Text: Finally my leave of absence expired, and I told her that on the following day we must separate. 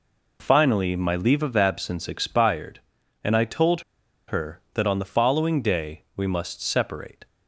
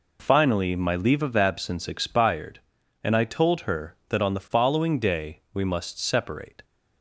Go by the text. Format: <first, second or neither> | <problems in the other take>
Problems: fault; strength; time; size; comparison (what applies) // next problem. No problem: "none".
second | pauses between "told" and "her"; noticeable; at 3.8 s; 0.46 s long